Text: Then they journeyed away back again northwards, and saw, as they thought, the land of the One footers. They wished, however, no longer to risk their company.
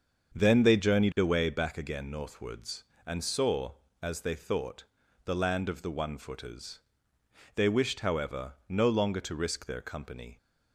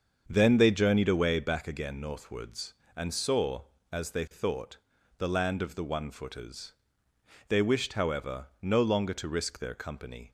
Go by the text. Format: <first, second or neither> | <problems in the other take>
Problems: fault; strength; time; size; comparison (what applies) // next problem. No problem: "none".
neither | starts louder than the rest; the same in both